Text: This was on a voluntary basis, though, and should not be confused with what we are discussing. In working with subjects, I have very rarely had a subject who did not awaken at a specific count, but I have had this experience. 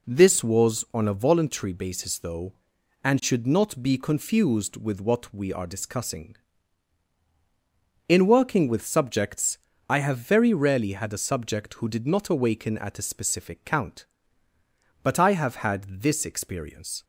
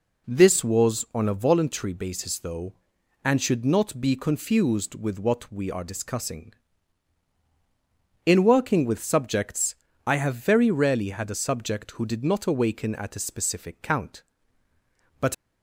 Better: first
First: none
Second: stops before "I have had this experience"; at 15.3 s

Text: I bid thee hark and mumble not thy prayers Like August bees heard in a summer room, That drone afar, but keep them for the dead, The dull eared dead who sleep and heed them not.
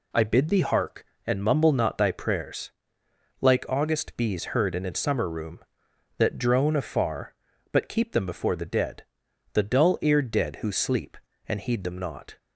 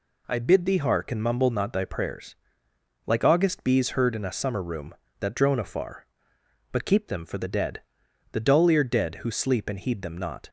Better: second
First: pauses between "prayers" and "Like"; noticeable; at 2.7 s; 0.70 s long // says "before" for "for"; at 8.2 s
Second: pauses between "prayers" and "Like"; noticeable; at 2.3 s; 0.70 s long

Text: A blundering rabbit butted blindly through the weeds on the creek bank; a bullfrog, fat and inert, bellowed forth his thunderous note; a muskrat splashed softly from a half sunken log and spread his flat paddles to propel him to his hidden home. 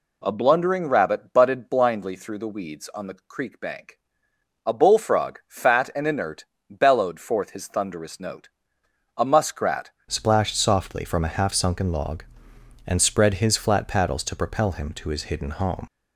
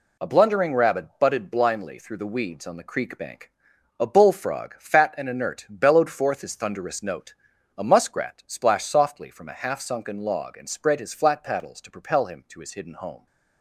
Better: second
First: changes voice at "splashed"; from 10.0 s on; 5.8 s long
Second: none

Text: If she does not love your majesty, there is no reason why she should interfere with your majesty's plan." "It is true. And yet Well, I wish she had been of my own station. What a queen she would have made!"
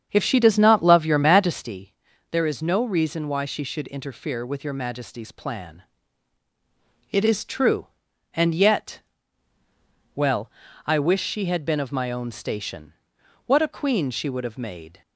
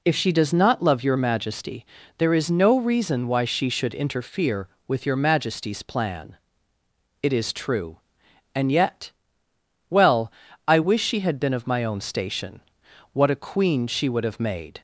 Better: second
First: starts louder than the rest; strong; until 1.8 s; 7.5 dB // pauses between "yet" and "Well"; at 9.0 s; 1.1 s long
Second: pauses between "yet" and "Well"; noticeable; at 9.1 s; 0.76 s long

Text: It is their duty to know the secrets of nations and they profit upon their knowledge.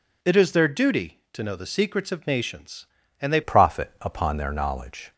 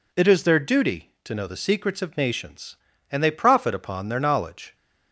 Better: second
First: changes voice at "profit"; from 3.4 s on; 1.7 s long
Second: none

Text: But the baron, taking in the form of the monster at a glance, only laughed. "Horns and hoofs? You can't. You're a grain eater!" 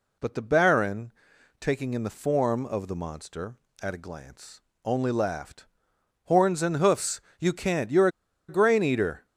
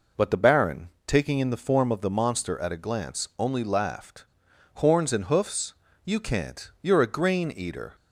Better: second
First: pauses between "You're" and "a"; at 8.0 s; 0.40 s long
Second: none

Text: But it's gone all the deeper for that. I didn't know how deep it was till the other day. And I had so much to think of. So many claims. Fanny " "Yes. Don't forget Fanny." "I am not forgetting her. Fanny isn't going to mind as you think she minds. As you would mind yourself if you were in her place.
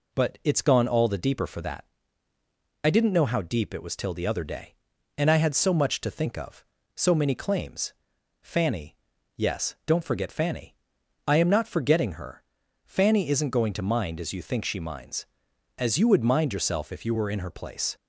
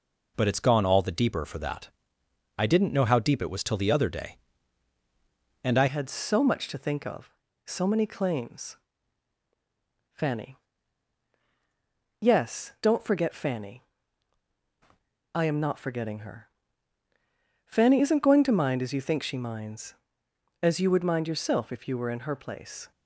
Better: first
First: none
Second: changes voice at "had"; from 5.8 s on; 17.1 s long

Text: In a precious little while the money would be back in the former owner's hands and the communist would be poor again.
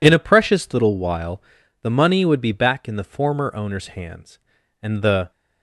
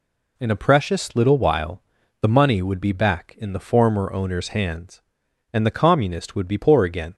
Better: second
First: pauses between "while" and "the"; at 1.4 s; 0.40 s long // stops before "communist would be poor again"; at 5.3 s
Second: pauses between "while" and "the"; at 1.8 s; 0.38 s long

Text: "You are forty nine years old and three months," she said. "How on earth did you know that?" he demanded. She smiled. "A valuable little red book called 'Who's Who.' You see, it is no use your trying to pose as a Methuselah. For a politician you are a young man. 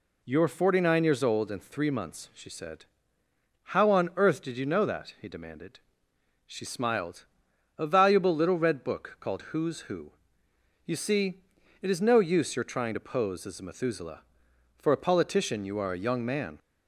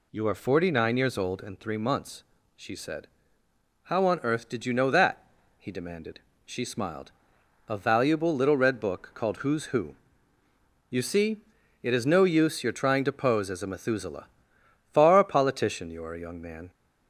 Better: first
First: none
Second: says "Far" for "For"; at 14.9 s

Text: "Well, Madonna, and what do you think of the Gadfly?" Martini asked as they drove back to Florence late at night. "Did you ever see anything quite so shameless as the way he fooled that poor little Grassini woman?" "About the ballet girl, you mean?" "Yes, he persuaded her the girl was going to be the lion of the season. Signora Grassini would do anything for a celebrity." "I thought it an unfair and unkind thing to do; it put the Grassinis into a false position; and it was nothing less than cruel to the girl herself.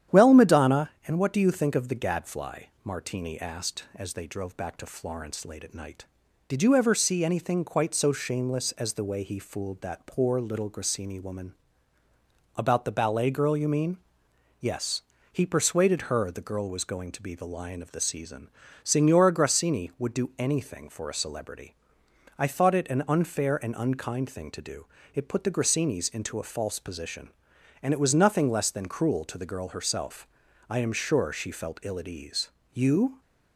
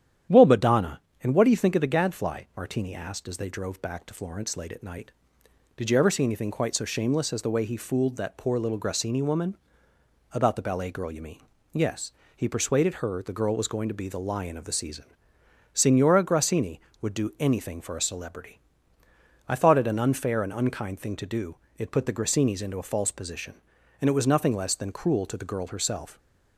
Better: second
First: starts louder than the rest; strong; until 1.2 s; 10 dB // goes on to say "I am sure she felt ill at ease You"; strong; from 30.6 s on; 2.5 s long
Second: starts louder than the rest; strong; until 1.5 s; 10 dB

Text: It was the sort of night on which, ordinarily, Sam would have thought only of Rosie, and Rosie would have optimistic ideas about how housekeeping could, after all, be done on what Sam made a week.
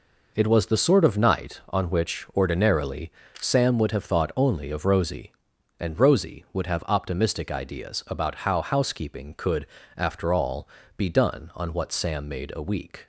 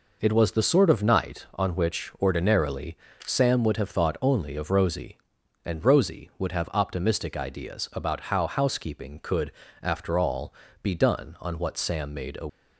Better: first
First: none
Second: stops before "week"; at 12.4 s

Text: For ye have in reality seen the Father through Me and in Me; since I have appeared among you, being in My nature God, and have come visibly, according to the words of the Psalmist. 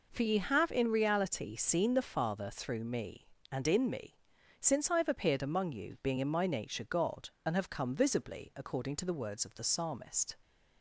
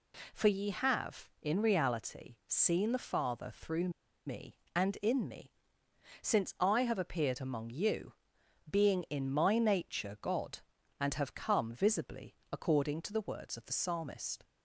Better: first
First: none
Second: pauses between "through" and "Me"; at 3.8 s; 0.37 s long

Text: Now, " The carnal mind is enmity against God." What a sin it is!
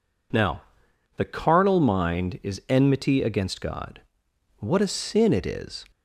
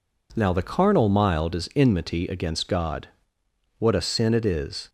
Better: first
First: none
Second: says "mild" for "mind"; at 1.0 s

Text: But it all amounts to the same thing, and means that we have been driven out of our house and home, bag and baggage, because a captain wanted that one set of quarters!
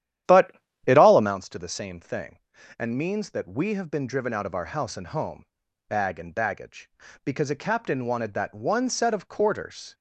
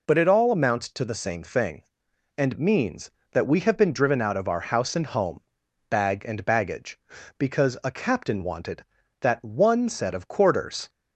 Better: second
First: starts louder than the rest; strong; until 1.3 s; 11 dB // pauses between "But" and "it"; slight; at 0.5 s; 0.36 s long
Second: none

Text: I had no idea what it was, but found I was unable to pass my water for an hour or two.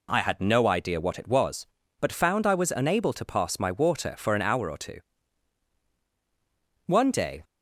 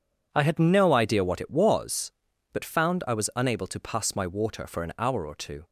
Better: second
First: goes on to say "One day"; from 6.8 s on; 0.56 s long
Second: none

